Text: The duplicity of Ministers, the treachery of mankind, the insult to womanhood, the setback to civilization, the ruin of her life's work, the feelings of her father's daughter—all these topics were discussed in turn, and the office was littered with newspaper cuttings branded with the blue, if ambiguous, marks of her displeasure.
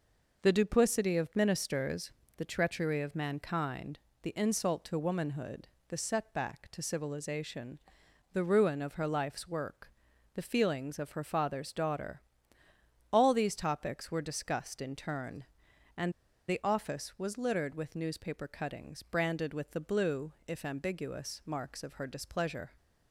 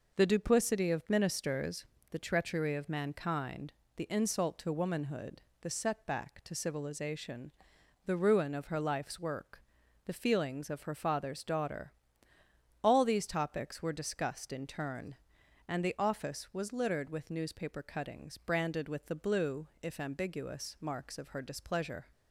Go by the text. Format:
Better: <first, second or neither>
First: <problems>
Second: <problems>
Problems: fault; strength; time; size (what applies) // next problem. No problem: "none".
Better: second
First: pauses between "and" and "the"; at 16.1 s; 0.37 s long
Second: none